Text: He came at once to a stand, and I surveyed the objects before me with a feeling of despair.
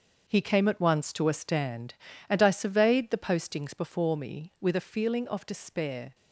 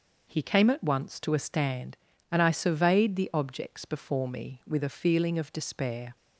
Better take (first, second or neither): second